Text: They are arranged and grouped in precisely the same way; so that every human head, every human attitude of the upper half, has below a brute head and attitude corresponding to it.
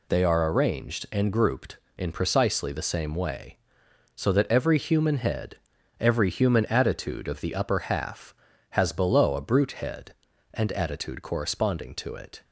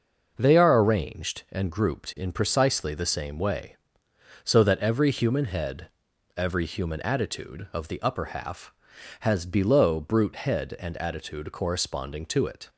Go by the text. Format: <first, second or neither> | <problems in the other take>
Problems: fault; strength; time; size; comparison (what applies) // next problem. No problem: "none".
first | skips "a"; at 9.9 s